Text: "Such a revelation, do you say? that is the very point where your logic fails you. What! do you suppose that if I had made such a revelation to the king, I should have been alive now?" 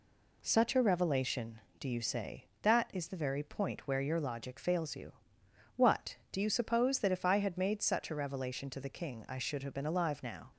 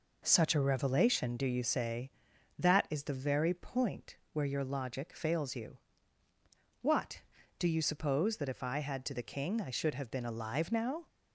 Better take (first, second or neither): first